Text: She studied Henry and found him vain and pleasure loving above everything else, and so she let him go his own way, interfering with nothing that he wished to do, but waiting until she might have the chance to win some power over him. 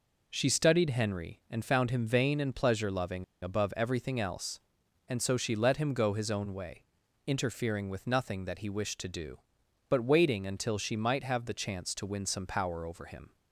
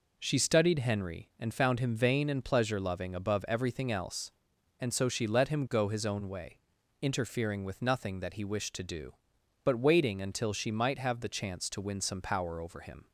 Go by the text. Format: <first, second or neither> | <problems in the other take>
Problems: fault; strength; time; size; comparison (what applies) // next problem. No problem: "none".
second | pauses between "loving" and "above"; slight; at 3.2 s; 0.18 s long